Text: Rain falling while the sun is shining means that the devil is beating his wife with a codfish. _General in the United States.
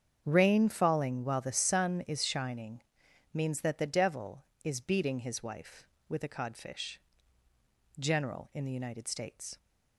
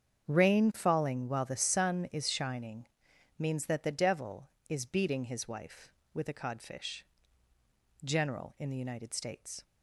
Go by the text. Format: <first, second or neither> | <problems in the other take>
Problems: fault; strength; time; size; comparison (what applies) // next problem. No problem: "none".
neither | starts louder than the rest; strong; the same in both // pauses between "shining" and "means"; noticeable; the same in both